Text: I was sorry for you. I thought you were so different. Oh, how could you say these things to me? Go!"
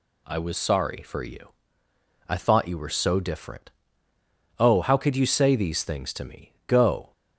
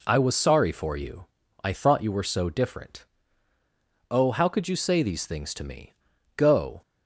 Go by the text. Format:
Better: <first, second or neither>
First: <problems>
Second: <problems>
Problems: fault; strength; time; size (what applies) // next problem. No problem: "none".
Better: neither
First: none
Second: none